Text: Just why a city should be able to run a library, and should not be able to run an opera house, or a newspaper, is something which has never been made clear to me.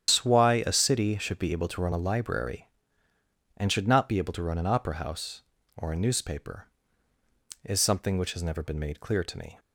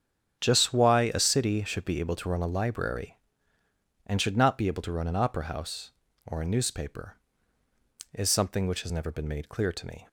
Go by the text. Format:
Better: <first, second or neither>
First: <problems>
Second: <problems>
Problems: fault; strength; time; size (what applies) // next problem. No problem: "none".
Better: second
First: loses the start of "Just"; at 0.0 s; 150 ms // starts louder than the rest; strong; until 1.1 s; 9.5 dB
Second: starts louder than the rest; strong; until 1.4 s; 8 dB